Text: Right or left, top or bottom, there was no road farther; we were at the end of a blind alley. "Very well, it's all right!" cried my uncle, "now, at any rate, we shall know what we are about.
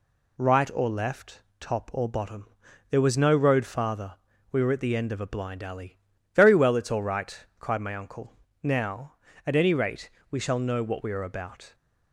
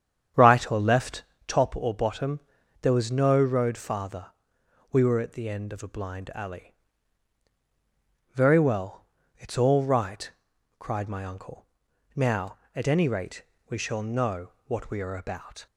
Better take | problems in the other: first | starts louder than the rest; strong; until 1.5 s; 8.5 dB // pauses between "know" and "what"; slight; at 14.5 s; 0.16 s long

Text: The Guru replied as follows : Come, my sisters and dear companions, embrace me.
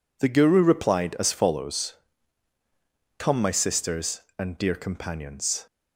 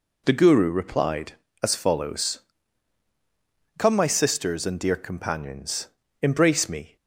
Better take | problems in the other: second | stops before "embrace me"; at 5.6 s

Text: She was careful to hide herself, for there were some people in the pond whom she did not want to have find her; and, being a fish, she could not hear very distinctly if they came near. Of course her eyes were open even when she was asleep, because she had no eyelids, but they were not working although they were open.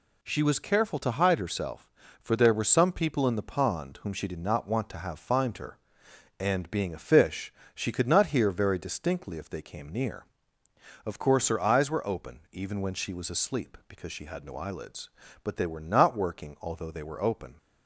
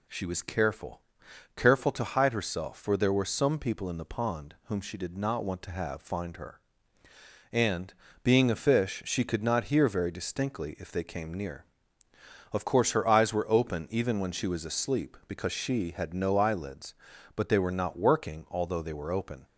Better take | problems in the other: first | says "careful" twice; at 1.5 s

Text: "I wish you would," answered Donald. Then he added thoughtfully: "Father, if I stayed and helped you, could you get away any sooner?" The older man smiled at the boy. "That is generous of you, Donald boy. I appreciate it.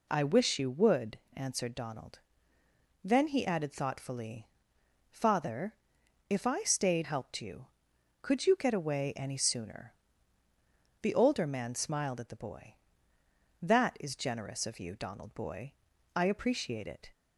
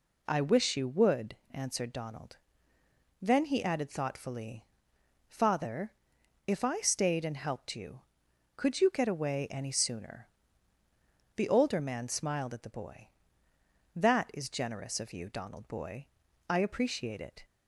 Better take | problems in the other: second | skips "and"; at 7.0 s

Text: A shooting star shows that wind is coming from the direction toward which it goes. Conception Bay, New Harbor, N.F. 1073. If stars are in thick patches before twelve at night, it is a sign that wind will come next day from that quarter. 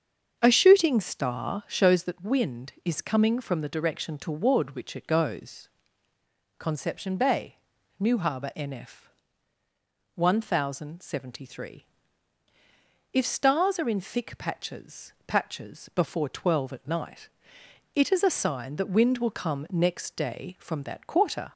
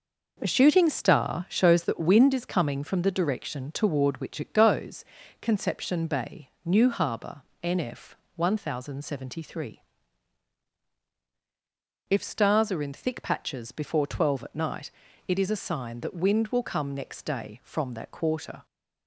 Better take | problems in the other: second | starts louder than the rest; until 1.4 s; 7 dB // says "patches" twice; at 15.2 s

